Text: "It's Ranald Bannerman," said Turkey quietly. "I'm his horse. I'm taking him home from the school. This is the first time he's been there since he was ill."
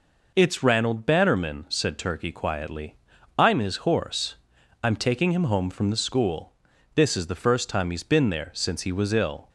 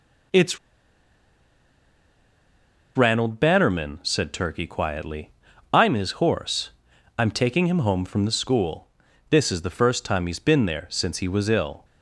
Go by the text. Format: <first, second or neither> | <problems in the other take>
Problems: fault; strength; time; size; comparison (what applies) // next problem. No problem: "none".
first | pauses between "It's" and "Ranald"; strong; at 0.5 s; 2.3 s long